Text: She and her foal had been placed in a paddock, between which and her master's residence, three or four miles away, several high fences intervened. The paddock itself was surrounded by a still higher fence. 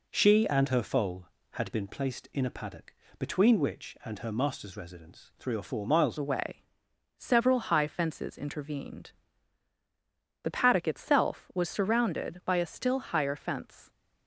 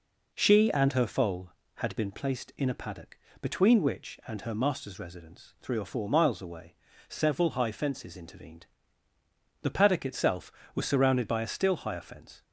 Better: second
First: changes voice at "away"; from 6.1 s on; 7.7 s long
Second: none

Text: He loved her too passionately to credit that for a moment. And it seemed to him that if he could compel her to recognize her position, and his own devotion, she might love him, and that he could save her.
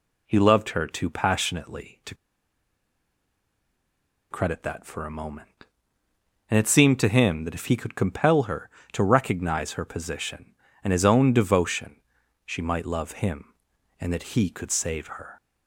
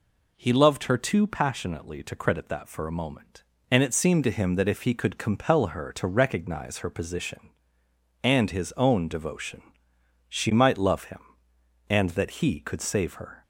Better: second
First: pauses between "to" and "credit"; strong; at 2.1 s; 2.1 s long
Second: none

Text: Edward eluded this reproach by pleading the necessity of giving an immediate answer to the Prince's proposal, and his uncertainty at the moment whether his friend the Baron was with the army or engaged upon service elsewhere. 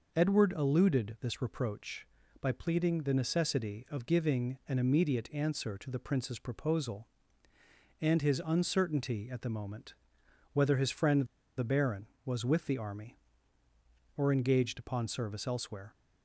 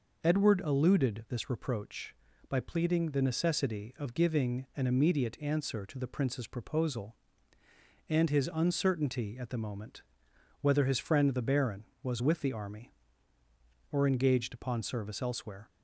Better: second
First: pauses between "moment" and "whether"; noticeable; at 9.9 s; 0.60 s long // pauses between "friend" and "the"; slight; at 11.2 s; 0.32 s long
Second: pauses between "moment" and "whether"; noticeable; at 10.0 s; 0.60 s long

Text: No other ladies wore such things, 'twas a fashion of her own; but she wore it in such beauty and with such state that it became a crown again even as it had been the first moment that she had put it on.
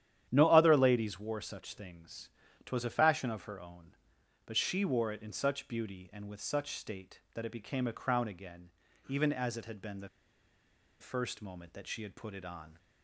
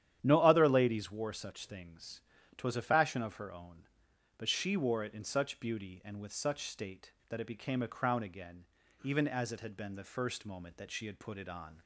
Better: second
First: starts louder than the rest; strong; until 1.3 s; 10.5 dB // pauses between "again" and "even"; at 8.6 s; 0.38 s long // pauses between "the" and "first"; noticeable; at 10.0 s; 0.92 s long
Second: starts louder than the rest; strong; until 1.2 s; 10.5 dB // pauses between "again" and "even"; at 8.6 s; 0.38 s long

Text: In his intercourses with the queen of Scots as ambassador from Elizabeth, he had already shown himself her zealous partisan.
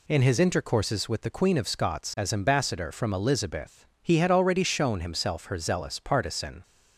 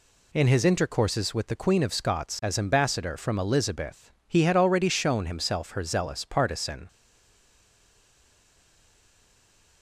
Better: first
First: none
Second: stays silent after the last word; strong; from 6.8 s on; 3.0 s long

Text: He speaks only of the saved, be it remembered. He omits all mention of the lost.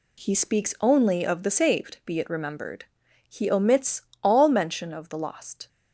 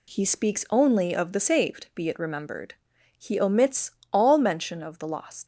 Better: first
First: pauses between "omits" and "all"; slight; at 4.0 s; 0.22 s long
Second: pauses between "omits" and "all"; slight; at 3.9 s; 0.22 s long // leaves "lost" unfinished; at 5.4 s; 105 ms

